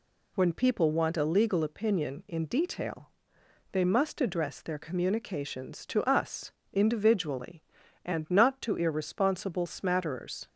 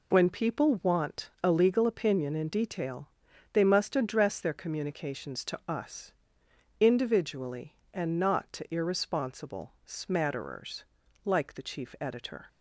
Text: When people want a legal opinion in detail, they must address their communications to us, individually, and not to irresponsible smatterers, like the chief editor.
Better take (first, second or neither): second